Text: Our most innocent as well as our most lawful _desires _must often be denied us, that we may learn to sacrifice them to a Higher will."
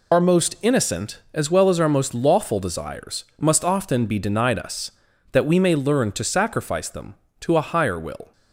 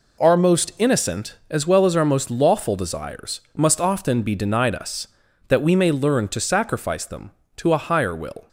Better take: second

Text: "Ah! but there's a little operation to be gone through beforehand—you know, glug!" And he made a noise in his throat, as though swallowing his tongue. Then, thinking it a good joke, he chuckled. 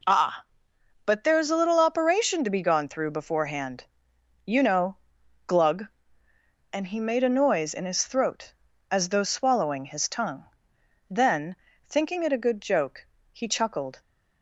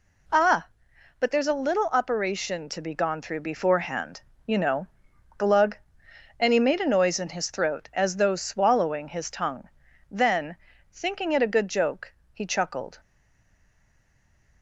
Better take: first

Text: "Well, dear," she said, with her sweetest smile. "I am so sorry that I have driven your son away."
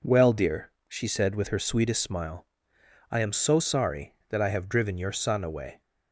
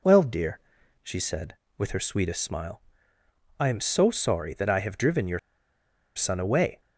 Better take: first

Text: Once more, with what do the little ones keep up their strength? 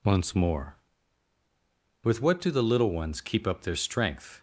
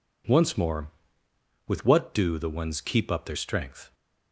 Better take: first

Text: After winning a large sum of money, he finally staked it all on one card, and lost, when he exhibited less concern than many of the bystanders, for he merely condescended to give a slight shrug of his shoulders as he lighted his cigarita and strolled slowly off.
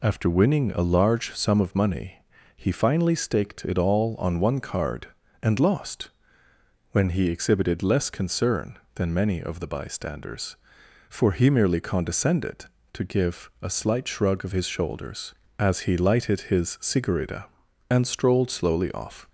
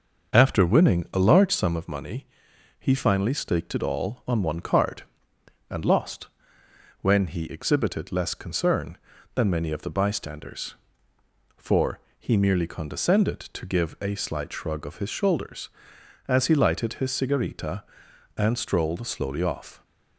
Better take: first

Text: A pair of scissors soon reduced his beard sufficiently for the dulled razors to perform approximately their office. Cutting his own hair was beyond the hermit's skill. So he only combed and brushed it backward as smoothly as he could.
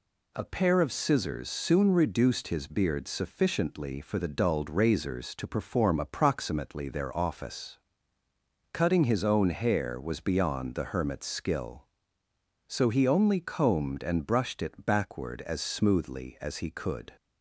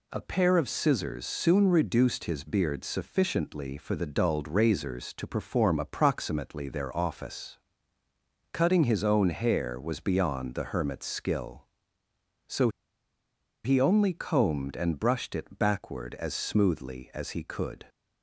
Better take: first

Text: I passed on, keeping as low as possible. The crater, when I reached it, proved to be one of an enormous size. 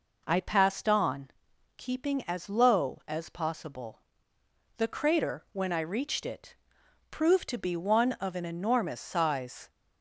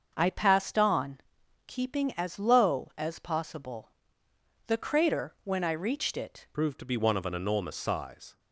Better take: first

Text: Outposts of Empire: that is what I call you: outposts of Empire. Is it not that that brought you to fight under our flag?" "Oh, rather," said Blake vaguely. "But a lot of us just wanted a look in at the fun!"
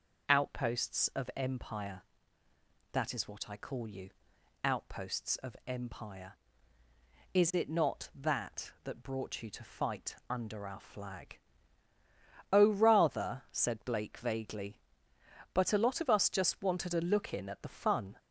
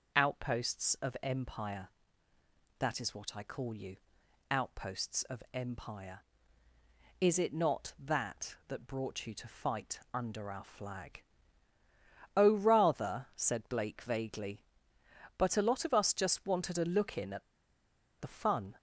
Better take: first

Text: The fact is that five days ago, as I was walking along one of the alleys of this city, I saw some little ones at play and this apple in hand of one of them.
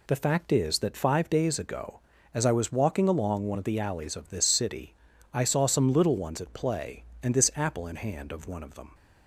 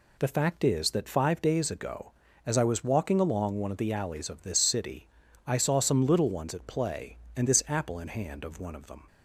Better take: neither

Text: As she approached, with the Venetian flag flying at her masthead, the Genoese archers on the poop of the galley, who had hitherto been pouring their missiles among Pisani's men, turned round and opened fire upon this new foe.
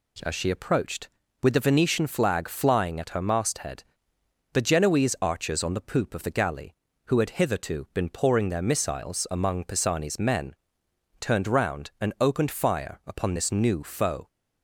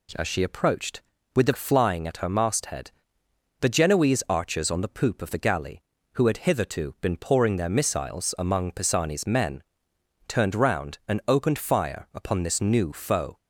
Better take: first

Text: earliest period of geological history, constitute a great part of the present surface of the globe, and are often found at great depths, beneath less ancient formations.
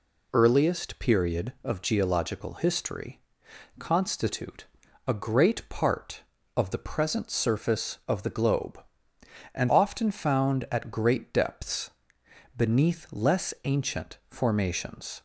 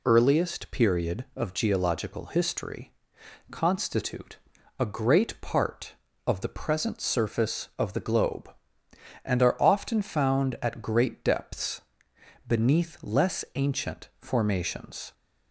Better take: second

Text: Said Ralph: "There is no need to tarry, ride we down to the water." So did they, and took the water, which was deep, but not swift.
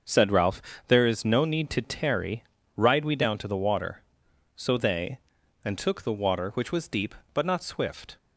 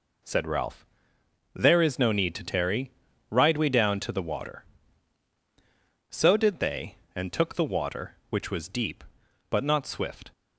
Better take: second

